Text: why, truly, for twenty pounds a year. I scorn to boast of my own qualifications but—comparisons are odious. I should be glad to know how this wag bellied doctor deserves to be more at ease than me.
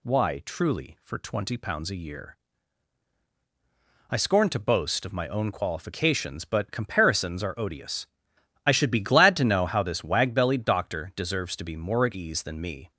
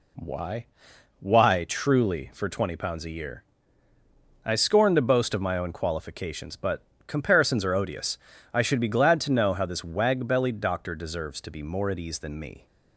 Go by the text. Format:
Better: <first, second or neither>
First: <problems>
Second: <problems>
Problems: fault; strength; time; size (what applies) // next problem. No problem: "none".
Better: first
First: none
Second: says "why" twice; at 1.1 s